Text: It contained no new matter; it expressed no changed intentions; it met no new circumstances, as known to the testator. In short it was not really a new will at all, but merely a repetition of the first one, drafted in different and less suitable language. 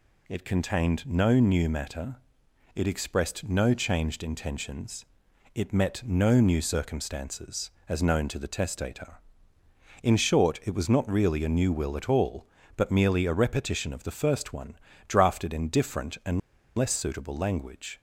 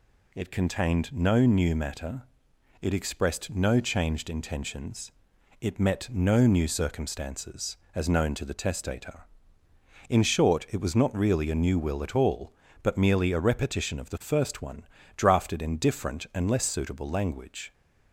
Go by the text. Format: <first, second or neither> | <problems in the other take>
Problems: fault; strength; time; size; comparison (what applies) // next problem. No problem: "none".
second | pauses between "and" and "less"; at 16.3 s; 0.38 s long